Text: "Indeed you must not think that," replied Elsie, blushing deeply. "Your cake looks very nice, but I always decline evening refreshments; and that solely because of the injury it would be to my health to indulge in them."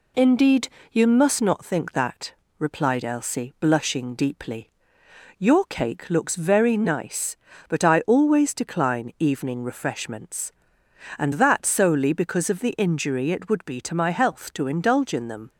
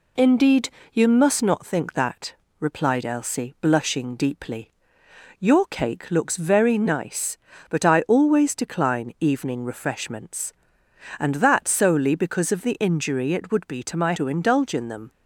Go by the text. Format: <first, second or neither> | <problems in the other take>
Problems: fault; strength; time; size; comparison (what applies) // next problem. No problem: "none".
first | pauses between "Indeed" and "you"; slight; at 0.6 s; 0.24 s long; slight in the first // skips "health"; at 14.1 s